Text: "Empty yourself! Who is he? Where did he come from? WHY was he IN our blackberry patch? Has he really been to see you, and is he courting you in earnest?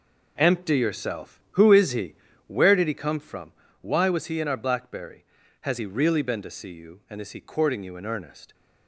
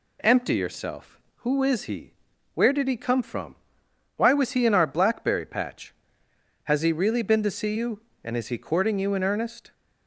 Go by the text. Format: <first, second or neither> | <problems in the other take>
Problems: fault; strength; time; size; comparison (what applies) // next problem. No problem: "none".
second | skips "patch"; at 5.4 s